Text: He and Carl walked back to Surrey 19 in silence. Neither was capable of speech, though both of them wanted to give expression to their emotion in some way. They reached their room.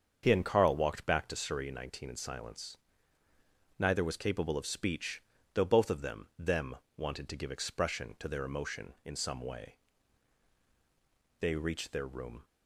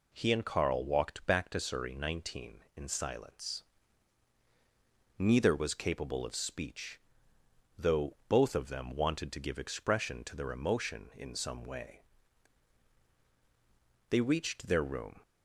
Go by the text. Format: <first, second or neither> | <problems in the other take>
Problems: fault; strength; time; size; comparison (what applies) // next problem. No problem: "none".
second | starts louder than the rest; until 1.2 s; 7 dB // says "them" twice; at 6.3 s